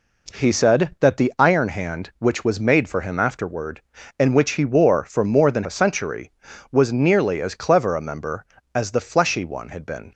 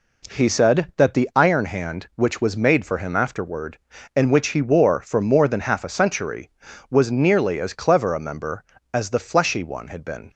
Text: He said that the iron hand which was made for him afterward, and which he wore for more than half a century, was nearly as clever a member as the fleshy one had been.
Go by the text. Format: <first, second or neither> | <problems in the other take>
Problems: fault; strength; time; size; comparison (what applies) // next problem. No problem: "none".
second | skips "half"; at 5.6 s